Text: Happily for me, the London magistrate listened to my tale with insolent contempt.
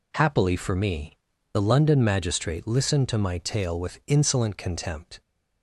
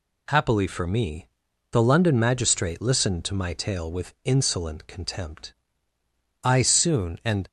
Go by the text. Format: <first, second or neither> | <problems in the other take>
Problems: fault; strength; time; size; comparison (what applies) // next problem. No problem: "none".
first | goes on to say "I soon and"; noticeable; from 6.4 s on; 1.0 s long